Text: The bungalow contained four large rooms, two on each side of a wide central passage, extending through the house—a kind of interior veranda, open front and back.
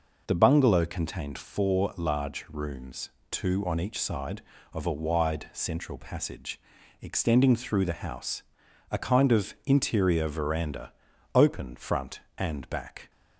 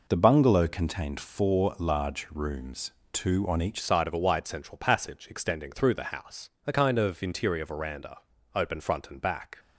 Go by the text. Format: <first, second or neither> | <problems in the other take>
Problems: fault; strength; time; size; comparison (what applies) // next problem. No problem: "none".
first | changes voice at "side"; from 3.8 s on; 5.7 s long